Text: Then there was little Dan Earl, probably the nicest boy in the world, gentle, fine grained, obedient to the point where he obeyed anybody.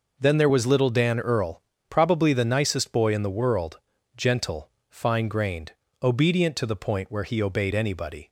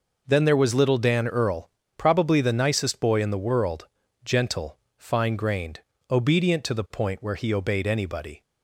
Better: neither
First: none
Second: none

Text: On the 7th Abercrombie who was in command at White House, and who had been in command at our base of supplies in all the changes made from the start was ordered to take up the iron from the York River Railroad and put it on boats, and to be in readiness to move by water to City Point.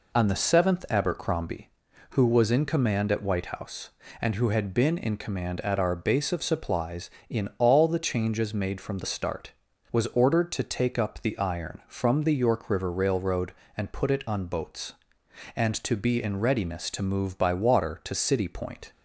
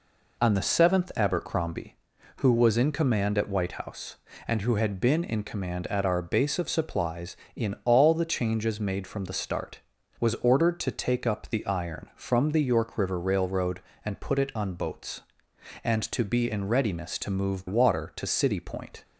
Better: first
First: none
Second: skips "by"; at 17.6 s

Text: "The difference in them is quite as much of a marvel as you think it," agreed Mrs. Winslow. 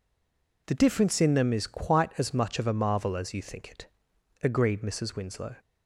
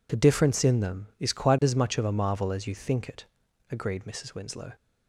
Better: second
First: stays silent before the first word; slight; until 0.6 s; 0.6 s long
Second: none

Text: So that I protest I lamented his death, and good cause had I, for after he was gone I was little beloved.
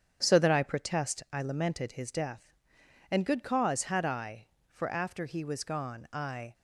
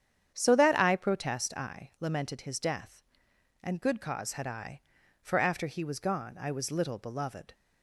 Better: second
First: starts louder than the rest; strong; until 1.2 s; 8 dB // stops before "was little beloved"; at 6.5 s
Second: starts louder than the rest; strong; until 1.3 s; 8.5 dB

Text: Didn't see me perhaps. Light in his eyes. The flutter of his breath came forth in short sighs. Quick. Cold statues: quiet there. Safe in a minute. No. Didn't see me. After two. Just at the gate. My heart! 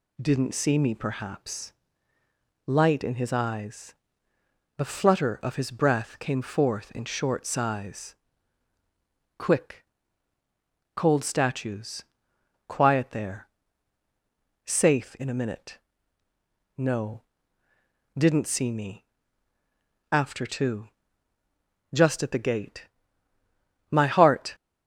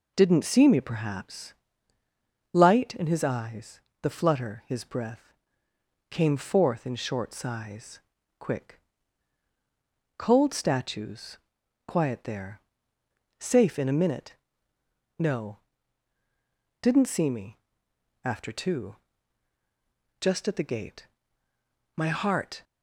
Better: first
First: none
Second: skips "of"; at 4.6 s // pauses between "breath" and "came"; noticeable; at 5.3 s; 0.78 s long

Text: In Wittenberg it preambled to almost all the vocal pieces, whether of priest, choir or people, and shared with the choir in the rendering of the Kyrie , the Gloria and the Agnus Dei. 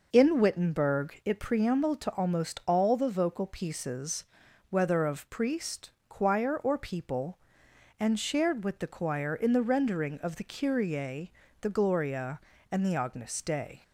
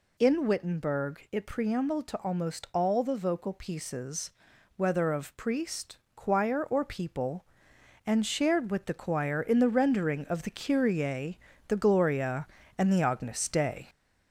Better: first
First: none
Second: gets louder; slight; throughout; 3.5 dB

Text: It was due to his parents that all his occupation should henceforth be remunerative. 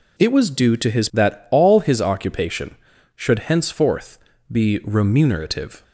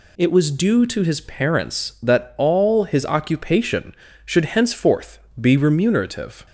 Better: second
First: skips "parents"; at 1.1 s // pauses between "henceforth" and "be"; slight; at 4.1 s; 0.34 s long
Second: pauses between "henceforth" and "be"; slight; at 5.1 s; 0.22 s long

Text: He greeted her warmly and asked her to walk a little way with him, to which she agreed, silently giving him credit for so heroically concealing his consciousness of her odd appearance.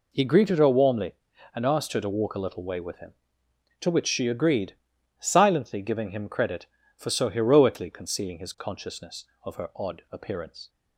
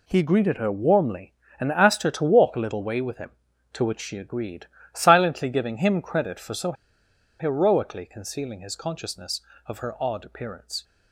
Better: first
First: none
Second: pauses between "so" and "heroically"; noticeable; at 6.7 s; 0.66 s long

